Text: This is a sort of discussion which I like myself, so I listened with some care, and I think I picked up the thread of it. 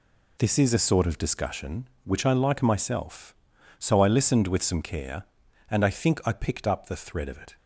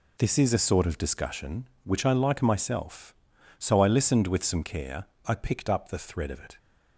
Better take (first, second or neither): first